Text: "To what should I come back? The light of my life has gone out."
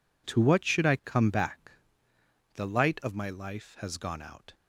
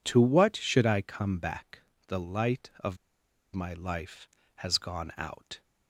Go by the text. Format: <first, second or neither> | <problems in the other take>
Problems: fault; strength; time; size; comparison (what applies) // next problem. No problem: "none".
first | pauses between "of" and "my"; noticeable; at 2.9 s; 0.58 s long